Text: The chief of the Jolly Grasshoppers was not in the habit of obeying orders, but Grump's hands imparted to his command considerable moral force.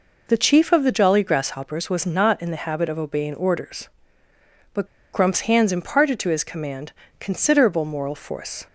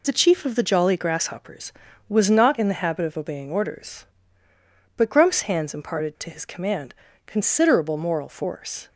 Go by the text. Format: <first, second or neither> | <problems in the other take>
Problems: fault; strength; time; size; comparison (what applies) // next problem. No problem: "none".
second | pauses between "but" and "Grump's"; slight; at 4.8 s; 0.28 s long // pauses between "command" and "considerable"; slight; at 6.9 s; 0.26 s long; slight in the second